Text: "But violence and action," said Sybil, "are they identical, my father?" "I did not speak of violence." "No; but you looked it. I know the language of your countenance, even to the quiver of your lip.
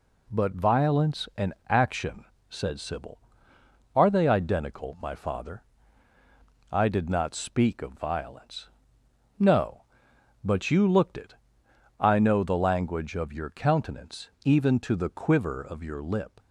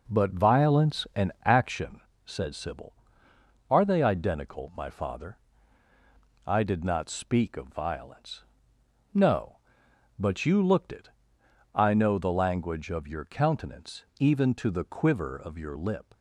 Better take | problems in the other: first | starts louder than the rest; noticeable; until 1.6 s; 4.5 dB

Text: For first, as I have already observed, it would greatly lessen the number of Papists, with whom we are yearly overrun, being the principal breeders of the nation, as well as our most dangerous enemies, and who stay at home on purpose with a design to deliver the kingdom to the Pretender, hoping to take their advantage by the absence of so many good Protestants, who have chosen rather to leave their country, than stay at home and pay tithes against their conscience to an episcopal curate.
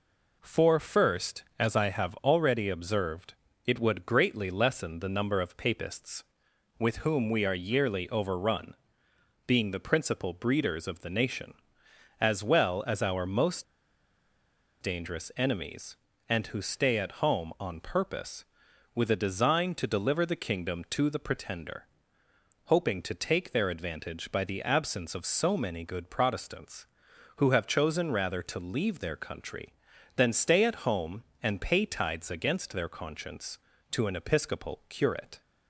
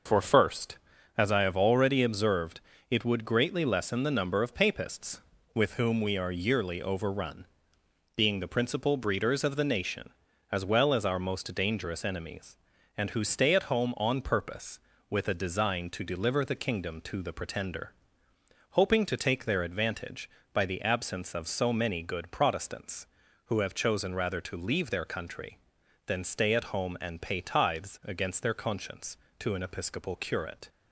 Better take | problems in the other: second | pauses between "most" and "dangerous"; at 13.6 s; 1.1 s long

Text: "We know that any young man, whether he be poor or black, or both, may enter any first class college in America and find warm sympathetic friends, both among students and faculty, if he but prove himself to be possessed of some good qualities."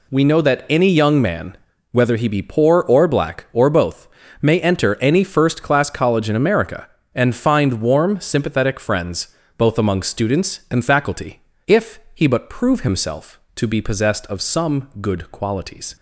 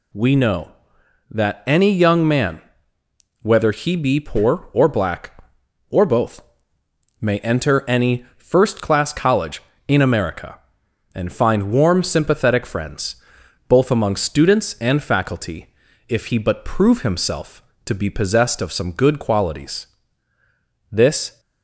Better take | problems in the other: first | goes on to say "This"; slight; from 20.9 s on; 0.48 s long

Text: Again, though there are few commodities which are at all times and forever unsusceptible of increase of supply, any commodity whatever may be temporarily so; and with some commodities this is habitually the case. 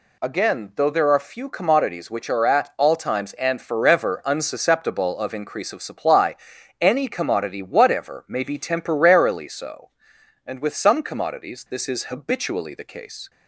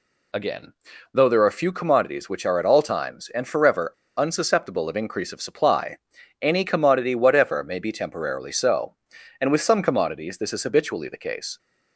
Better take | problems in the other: first | pauses between "forever" and "unsusceptible"; slight; at 3.9 s; 0.24 s long

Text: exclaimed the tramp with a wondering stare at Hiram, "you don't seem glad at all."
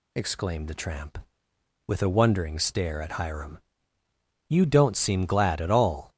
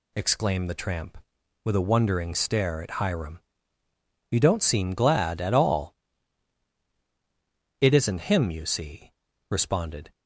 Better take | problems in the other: first | goes on to say "It isn't him you see responded"; strong; from 7.8 s on; 2.3 s long

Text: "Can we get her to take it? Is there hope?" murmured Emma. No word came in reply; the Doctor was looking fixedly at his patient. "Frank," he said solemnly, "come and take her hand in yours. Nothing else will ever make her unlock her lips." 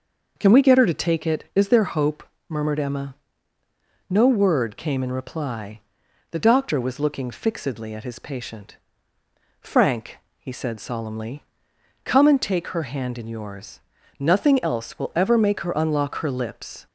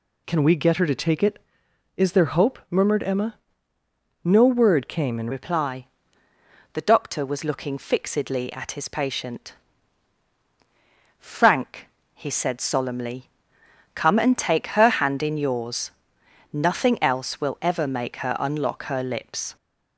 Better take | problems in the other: first | changes voice at "reply"; from 5.3 s on; 14.2 s long

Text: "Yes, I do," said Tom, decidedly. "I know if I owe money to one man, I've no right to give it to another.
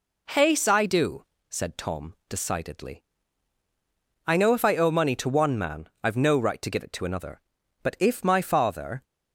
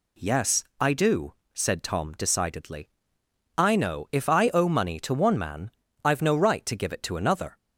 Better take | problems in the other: second | goes on to say "But if my father"; noticeable; from 7.8 s on; 1.2 s long

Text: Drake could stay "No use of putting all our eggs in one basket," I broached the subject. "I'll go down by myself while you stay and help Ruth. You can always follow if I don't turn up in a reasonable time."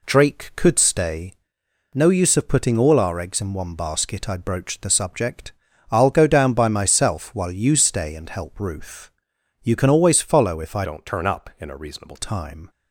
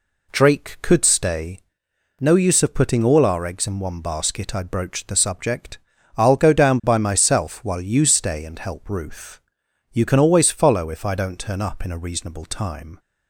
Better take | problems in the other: second | pauses between "stay" and "No"; noticeable; at 1.3 s; 0.60 s long; noticeable in the second // changes voice from "don't" to "reasonable"; from 10.8 to 12.1 s; 1.3 s long

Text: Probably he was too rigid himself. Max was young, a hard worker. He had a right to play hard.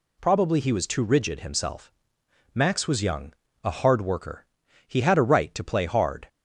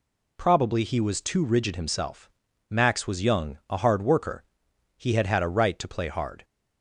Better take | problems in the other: first | says "had" twice; at 5.2 s

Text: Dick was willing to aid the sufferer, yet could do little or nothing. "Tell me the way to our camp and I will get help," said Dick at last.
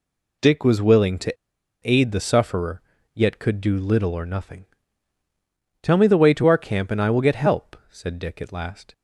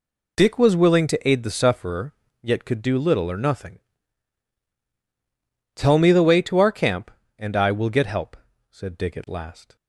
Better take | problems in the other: second | pauses between "to" and "aid"; noticeable; at 1.3 s; 0.47 s long

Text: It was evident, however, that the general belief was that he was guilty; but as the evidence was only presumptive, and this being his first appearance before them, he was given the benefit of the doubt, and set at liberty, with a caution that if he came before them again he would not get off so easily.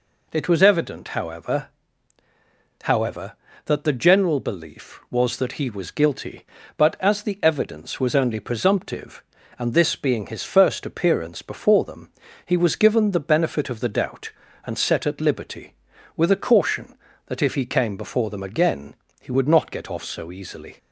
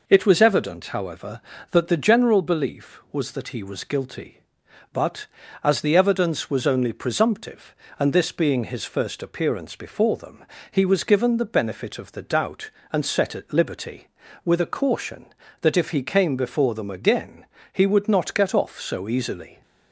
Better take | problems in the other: second | says "however" twice; at 2.8 s // pauses between "again" and "he"; slight; at 18.9 s; 0.28 s long; slight in the second

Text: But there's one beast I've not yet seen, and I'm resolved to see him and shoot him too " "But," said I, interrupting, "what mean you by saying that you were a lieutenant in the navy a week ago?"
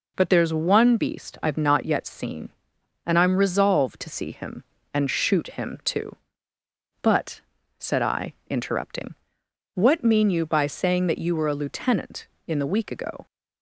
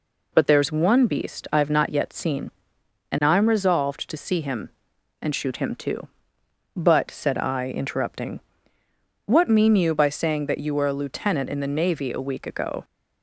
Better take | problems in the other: second | skips "navy a"; at 12.6 s

